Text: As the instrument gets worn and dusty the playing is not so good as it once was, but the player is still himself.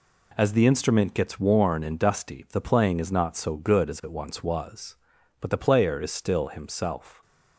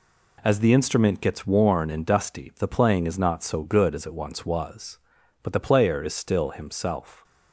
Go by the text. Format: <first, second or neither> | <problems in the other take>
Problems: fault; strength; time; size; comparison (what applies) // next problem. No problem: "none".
neither | none